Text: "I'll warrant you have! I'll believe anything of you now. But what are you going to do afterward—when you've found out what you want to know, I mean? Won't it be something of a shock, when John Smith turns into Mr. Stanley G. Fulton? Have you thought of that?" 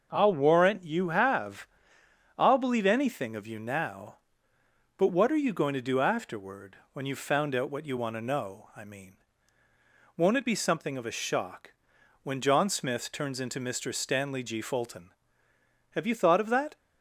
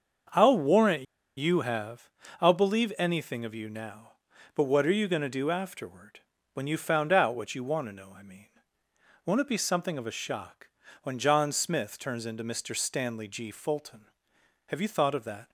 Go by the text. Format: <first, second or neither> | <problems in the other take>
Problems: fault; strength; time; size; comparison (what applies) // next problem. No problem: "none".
first | starts louder than the rest; until 1.6 s; 6.5 dB; noticeable in the first // pauses between "warrant" and "you"; slight; at 1.0 s; 0.32 s long